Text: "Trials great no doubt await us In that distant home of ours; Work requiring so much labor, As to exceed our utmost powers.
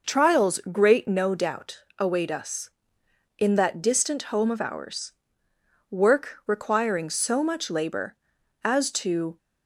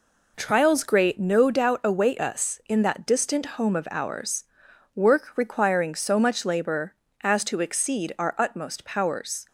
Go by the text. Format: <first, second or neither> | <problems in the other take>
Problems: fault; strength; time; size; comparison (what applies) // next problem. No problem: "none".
second | pauses between "doubt" and "await"; slight; at 1.8 s; 0.16 s long // stops before "exceed our utmost powers"; at 9.3 s